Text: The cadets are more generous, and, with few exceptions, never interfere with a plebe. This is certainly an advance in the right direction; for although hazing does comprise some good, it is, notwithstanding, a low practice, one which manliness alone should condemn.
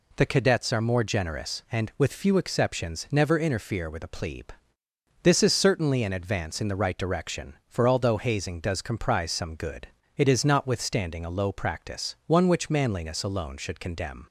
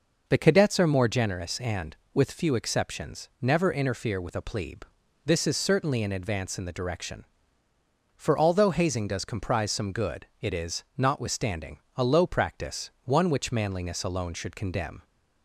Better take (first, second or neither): first